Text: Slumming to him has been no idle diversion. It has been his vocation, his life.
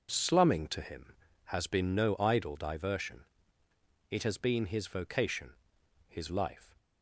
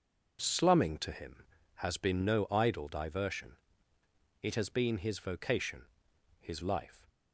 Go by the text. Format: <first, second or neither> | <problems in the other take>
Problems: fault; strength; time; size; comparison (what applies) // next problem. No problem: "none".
neither | none